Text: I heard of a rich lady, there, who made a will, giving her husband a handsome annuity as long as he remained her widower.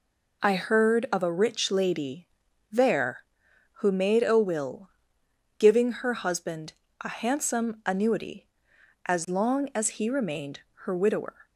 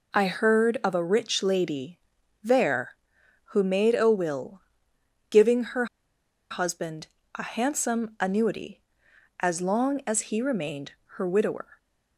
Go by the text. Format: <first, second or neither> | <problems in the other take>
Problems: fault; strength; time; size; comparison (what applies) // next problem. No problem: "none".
first | pauses between "her" and "husband"; noticeable; at 5.8 s; 0.65 s long // pauses between "husband" and "a"; slight; at 7.0 s; 0.30 s long; slight in the first // pauses between "remained" and "her"; slight; at 10.9 s; 0.24 s long; slight in the first